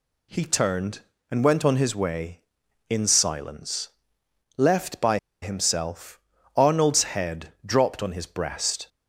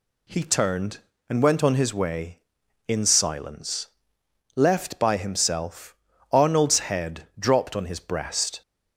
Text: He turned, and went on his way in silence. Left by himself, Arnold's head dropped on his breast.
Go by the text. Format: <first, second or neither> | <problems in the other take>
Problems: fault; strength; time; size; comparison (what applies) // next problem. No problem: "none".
second | pauses between "by" and "himself"; slight; at 5.1 s; 0.24 s long